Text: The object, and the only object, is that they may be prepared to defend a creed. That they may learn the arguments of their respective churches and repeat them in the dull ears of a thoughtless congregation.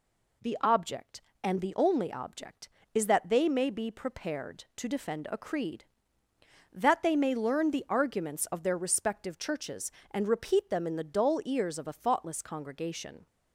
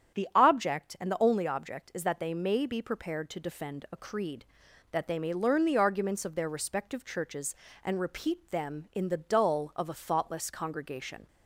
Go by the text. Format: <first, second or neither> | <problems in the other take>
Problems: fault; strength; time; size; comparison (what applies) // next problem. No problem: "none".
first | starts louder than the rest; strong; until 1.2 s; 9 dB // skips "ears"; at 9.7 s